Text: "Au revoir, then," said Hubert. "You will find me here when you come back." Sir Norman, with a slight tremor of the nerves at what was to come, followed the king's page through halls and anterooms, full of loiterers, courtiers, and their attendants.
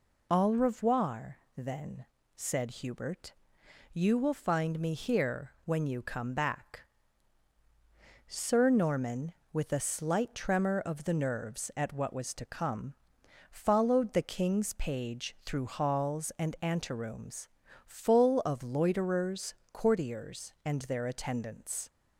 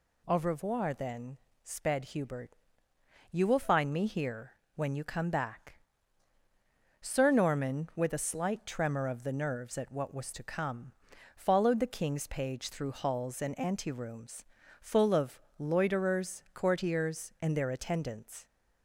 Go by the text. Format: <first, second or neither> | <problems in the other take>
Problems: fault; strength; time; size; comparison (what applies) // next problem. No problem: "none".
first | says "sped" for "said"; at 1.6 s // pauses between "here" and "when"; slight; at 4.5 s; 0.22 s long // pauses between "of" and "loiterers"; slight; at 15.4 s; 0.18 s long